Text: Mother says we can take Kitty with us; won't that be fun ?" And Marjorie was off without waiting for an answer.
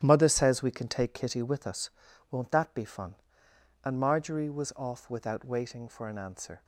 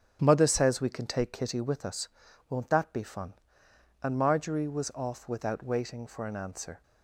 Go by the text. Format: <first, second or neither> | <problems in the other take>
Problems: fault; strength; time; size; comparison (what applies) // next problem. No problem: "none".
second | gets quieter; strong; throughout; 11 dB // starts louder than the rest; strong; until 1.0 s; 9 dB; also in the second